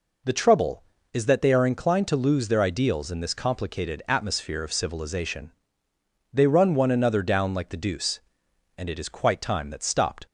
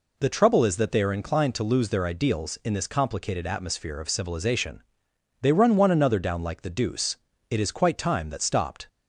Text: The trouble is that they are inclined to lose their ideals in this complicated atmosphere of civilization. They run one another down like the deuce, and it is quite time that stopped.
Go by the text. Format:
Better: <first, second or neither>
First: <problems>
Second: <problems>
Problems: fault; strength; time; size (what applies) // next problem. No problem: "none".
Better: first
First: none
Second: skips "and"; at 7.3 s